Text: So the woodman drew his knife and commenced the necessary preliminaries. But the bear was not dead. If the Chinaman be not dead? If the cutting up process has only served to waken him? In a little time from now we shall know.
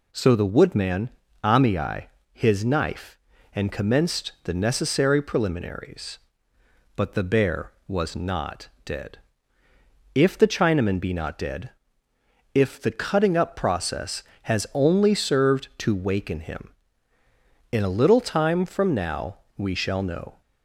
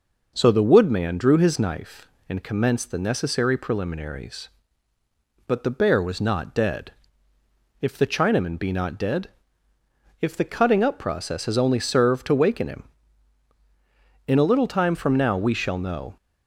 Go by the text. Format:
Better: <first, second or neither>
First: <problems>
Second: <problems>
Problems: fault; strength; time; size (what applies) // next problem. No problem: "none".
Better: second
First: says "amii" for "drew"; at 1.4 s // pauses between "not" and "dead"; slight; at 8.6 s; 0.16 s long // pauses between "now" and "we"; slight; at 19.3 s; 0.20 s long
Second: none